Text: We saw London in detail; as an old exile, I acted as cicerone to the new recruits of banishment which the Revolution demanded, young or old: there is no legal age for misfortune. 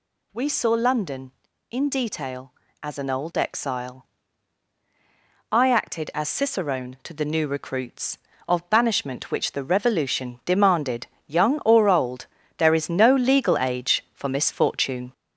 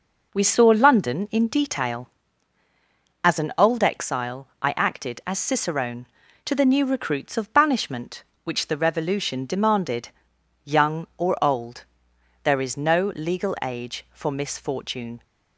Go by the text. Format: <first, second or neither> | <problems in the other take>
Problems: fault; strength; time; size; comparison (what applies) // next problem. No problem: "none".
second | gets louder; noticeable; throughout; 4.5 dB